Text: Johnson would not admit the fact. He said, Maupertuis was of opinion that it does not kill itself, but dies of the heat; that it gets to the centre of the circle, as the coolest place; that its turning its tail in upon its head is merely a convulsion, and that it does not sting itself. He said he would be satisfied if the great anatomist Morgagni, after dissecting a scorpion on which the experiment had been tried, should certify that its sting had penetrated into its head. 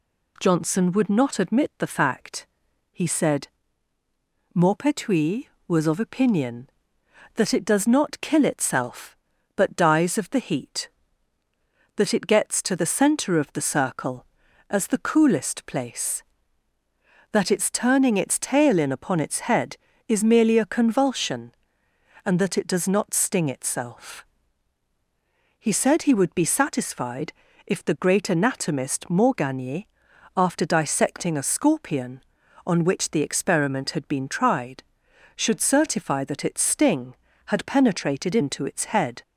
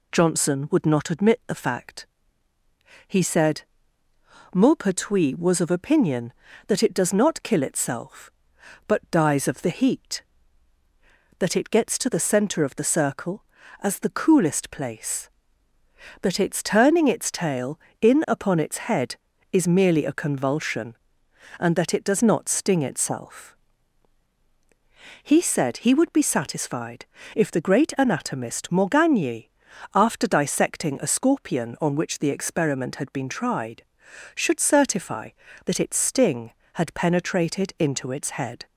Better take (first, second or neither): neither